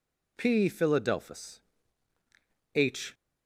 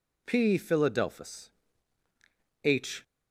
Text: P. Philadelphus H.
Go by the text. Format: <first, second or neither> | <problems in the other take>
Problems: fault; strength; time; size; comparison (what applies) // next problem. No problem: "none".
neither | pauses between "Philadelphus" and "H"; the same in both